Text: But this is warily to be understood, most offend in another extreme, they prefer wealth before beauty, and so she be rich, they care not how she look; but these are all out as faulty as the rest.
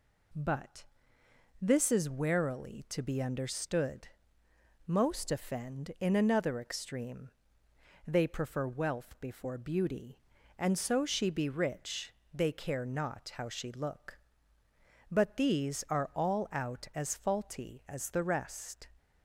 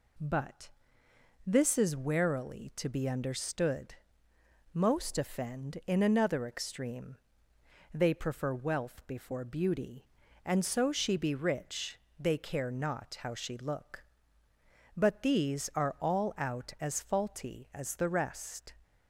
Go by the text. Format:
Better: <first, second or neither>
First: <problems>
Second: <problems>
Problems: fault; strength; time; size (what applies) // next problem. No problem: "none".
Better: neither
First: pauses between "But" and "this"; noticeable; at 0.8 s; 0.76 s long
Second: pauses between "But" and "this"; noticeable; at 0.6 s; 0.76 s long